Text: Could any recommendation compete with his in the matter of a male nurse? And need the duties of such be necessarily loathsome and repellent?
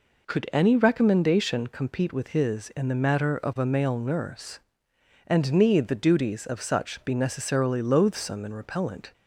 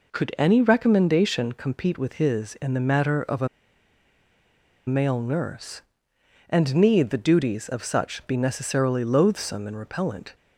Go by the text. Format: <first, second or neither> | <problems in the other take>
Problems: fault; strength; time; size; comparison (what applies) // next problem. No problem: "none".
first | pauses between "a" and "male"; strong; at 3.4 s; 1.3 s long